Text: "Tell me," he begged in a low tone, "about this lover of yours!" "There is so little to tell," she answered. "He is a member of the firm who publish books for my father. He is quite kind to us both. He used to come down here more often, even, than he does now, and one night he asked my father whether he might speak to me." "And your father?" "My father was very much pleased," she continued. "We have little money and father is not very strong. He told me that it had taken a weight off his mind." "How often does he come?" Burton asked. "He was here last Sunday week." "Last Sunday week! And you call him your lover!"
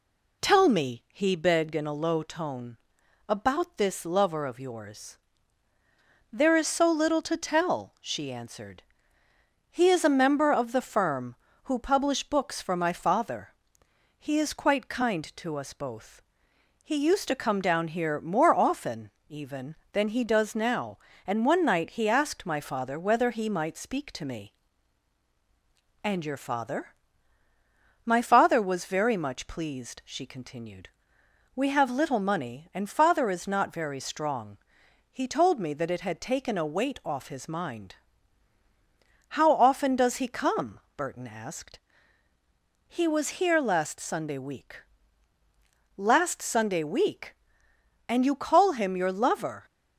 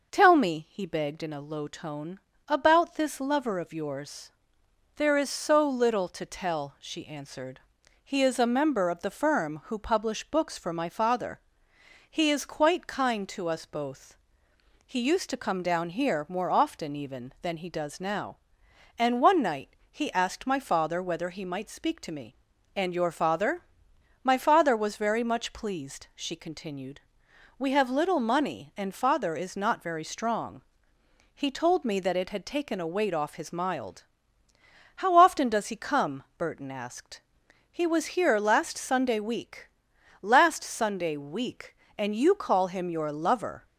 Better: first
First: none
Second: pauses between "night" and "he"; slight; at 19.7 s; 0.16 s long // says "mild" for "mind"; at 33.5 s

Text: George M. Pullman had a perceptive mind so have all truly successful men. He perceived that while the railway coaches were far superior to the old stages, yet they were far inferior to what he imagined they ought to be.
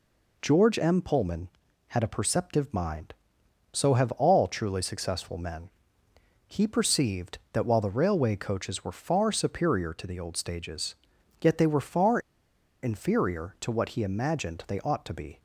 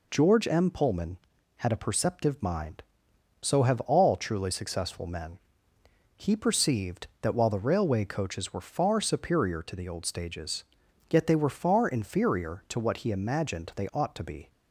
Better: second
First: pauses between "far" and "inferior"; noticeable; at 12.1 s; 0.63 s long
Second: none

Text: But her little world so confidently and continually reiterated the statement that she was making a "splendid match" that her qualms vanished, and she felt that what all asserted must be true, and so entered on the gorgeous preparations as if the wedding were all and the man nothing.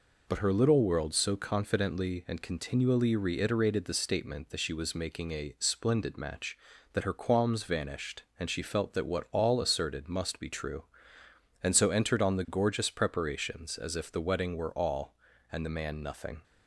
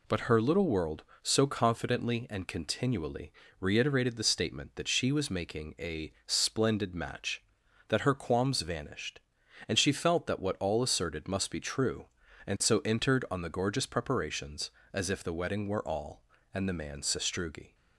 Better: first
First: none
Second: pauses between "continually" and "reiterated"; slight; at 3.3 s; 0.28 s long // pauses between "a" and "splendid"; slight; at 6.1 s; 0.16 s long // says "sastrugi" for "nothing"; at 17.0 s

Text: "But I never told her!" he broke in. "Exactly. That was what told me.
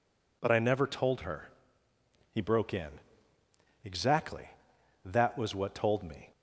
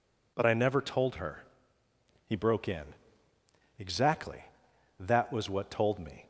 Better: neither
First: none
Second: none

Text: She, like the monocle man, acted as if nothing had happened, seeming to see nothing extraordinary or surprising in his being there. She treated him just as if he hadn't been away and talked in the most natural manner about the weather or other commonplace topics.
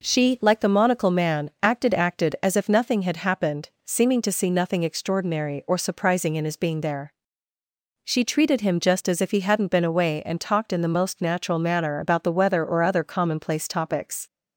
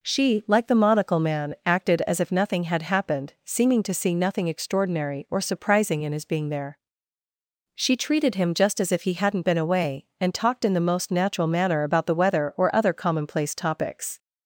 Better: second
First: says "acted" twice; at 1.9 s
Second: none

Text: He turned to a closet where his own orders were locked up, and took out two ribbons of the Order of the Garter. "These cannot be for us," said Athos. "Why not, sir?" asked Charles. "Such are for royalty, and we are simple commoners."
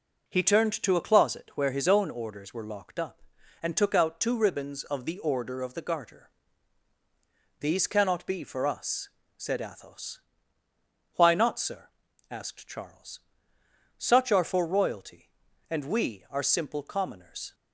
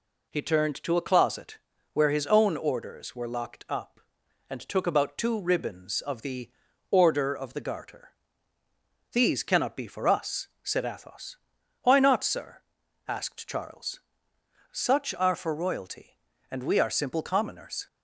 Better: first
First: none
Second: pauses between "closet" and "where"; slight; at 1.5 s; 0.36 s long // says "about" for "out"; at 4.8 s // pauses between "the" and "Order"; at 6.4 s; 0.42 s long

